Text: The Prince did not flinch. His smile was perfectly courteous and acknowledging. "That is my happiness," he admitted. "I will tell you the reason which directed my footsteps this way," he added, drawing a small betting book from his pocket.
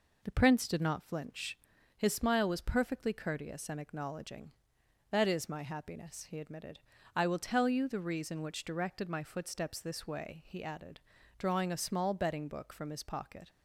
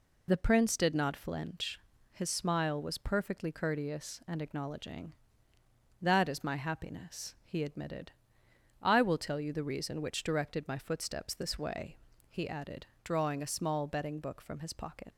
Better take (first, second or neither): first